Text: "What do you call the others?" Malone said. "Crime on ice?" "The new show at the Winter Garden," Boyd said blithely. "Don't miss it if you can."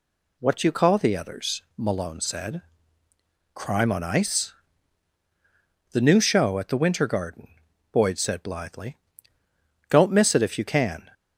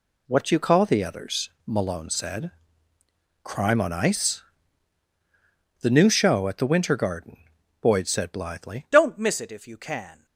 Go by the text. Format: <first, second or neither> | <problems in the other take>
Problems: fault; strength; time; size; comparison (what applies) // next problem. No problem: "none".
first | changes voice at "Don't"; from 8.9 s on; 1.3 s long